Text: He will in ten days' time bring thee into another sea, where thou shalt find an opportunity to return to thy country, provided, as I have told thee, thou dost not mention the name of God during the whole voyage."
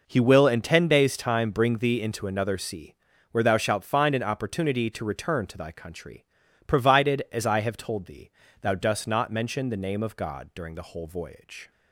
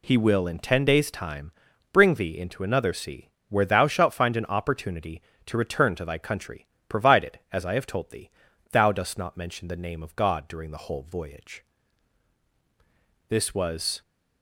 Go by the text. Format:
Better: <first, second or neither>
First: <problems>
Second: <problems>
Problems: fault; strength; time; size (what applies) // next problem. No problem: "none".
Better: first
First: none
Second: pauses between "time" and "bring"; at 1.5 s; 0.42 s long // goes on to say "This was"; noticeable; from 13.2 s on; 0.72 s long